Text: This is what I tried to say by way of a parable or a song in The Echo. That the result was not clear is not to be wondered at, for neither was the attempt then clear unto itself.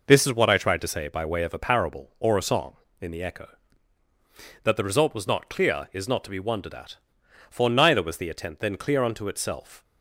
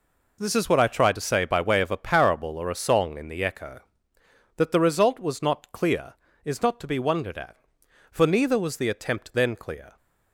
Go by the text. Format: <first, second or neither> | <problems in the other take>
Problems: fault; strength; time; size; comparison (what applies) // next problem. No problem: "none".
first | stops before "unto itself"; at 9.9 s